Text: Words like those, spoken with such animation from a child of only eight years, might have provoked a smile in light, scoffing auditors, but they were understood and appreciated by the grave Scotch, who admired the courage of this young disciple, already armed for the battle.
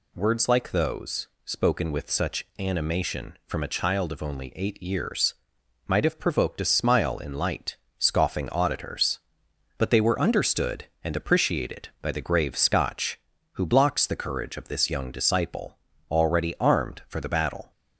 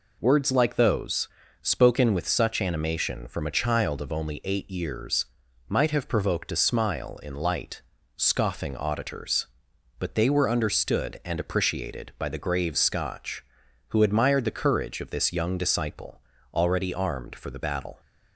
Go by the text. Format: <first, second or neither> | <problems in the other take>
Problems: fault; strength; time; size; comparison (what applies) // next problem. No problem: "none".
second | says "blocks" for "admired"; at 13.6 s